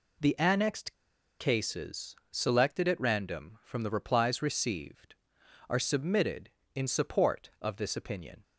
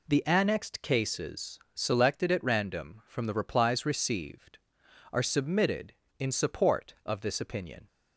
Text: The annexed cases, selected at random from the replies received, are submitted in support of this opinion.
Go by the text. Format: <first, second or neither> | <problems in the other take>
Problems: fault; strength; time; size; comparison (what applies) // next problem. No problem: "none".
second | pauses between "annexed" and "cases"; at 0.9 s; 0.44 s long